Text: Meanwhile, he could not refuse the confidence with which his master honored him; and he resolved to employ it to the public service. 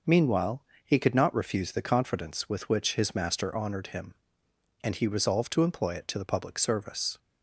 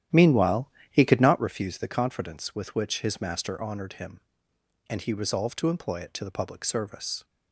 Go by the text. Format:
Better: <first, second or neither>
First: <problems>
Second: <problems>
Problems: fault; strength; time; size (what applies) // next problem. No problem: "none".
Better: first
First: none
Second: starts louder than the rest; strong; until 1.5 s; 11.5 dB